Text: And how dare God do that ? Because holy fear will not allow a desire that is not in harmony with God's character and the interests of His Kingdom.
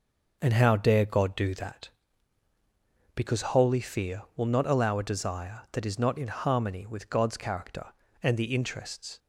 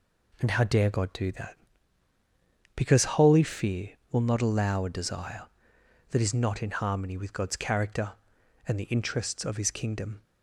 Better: second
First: stops before "of His Kingdom"; at 9.1 s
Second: none

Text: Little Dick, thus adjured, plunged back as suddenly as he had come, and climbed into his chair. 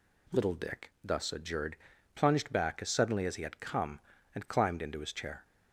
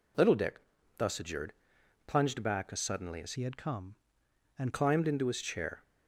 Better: first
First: none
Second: changes voice from "he" to "and"; from 3.3 to 4.7 s; 1.4 s long

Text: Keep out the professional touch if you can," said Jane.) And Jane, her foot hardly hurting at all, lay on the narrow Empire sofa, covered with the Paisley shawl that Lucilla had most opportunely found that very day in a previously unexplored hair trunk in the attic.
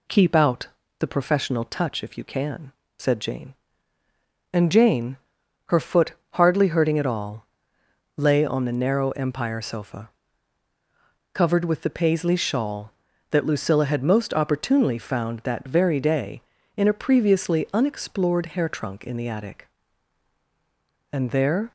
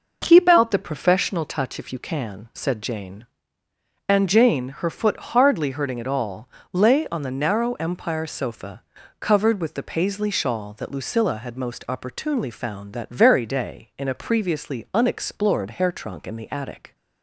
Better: second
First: pauses between "out" and "the"; slight; at 0.6 s; 0.32 s long // pauses between "foot" and "hardly"; slight; at 6.1 s; 0.18 s long // goes on to say "And there"; from 21.1 s on; 0.60 s long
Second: none

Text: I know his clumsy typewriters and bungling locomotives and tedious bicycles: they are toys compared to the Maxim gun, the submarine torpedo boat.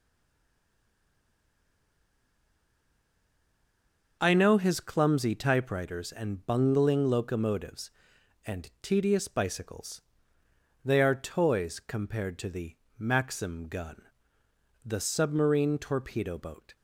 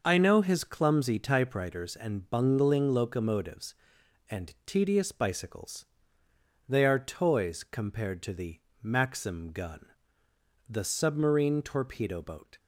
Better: second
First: stays silent before the first word; strong; until 4.2 s; 4.2 s long // pauses between "the" and "Maxim"; slight; at 12.7 s; 0.22 s long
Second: pauses between "the" and "Maxim"; slight; at 8.5 s; 0.22 s long

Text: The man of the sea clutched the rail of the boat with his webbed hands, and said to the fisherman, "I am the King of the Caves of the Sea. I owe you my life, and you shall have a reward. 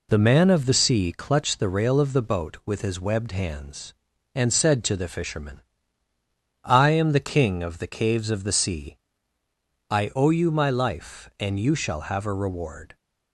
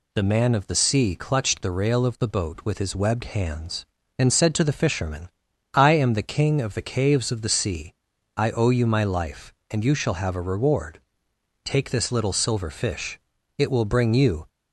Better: first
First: none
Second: goes on to say "Take this little silver fish It will bring you"; strong; from 11.6 s on; 2.8 s long

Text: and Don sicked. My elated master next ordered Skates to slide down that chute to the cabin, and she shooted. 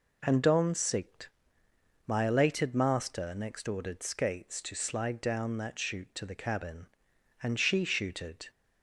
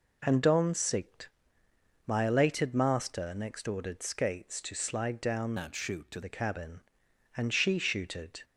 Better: first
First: none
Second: changes voice from "that" to "to"; from 5.5 to 6.2 s; 0.7 s long

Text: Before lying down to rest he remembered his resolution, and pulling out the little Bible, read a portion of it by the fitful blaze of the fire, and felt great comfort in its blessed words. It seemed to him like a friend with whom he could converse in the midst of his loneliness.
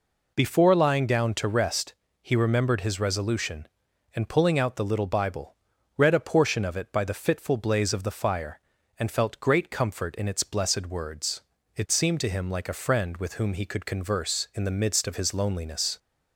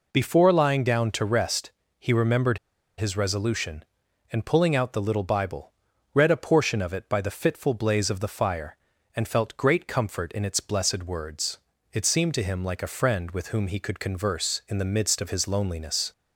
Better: first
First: pauses between "rest" and "he"; slight; at 1.9 s; 0.28 s long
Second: pauses between "rest" and "he"; slight; at 1.7 s; 0.28 s long // pauses between "remembered" and "his"; at 2.5 s; 0.39 s long

